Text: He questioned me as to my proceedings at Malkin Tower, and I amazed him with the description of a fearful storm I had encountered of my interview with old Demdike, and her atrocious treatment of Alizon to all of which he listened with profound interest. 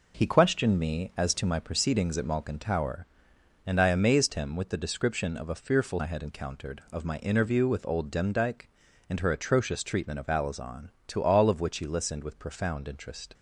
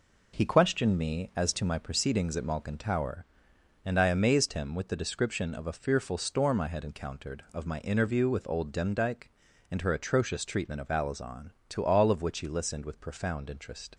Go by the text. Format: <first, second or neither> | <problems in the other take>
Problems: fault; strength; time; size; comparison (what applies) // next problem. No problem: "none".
second | skips "storm"; at 5.9 s